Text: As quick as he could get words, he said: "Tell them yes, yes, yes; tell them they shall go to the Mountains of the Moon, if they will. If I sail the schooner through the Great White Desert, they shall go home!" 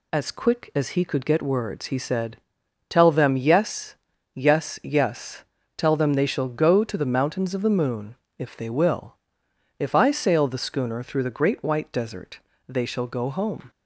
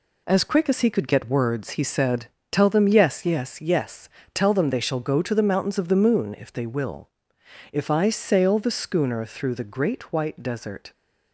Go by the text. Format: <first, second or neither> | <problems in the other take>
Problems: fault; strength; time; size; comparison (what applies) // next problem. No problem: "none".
first | stops before "they shall go home"; at 10.9 s